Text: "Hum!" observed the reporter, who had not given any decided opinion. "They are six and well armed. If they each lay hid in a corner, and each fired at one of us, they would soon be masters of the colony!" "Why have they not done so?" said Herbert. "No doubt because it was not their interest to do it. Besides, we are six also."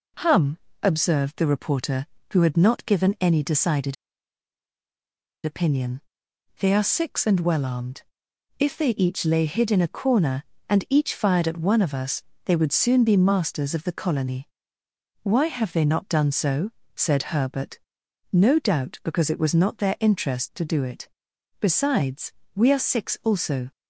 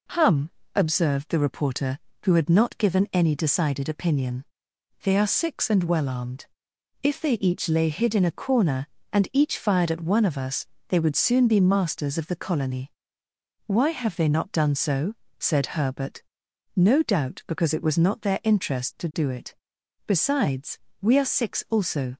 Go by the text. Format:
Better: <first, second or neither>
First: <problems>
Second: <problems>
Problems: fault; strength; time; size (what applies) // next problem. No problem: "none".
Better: second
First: pauses between "decided" and "opinion"; strong; at 3.9 s; 1.4 s long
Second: none